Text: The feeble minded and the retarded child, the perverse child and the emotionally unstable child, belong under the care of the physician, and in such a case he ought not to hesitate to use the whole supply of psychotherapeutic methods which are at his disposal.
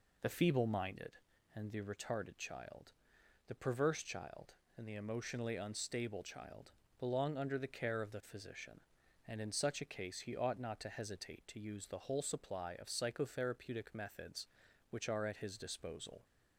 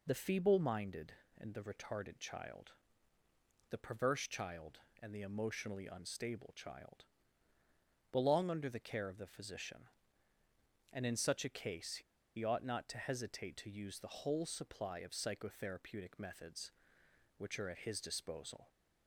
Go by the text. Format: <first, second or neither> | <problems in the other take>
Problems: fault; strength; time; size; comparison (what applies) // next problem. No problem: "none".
first | pauses between "case" and "he"; at 11.9 s; 0.36 s long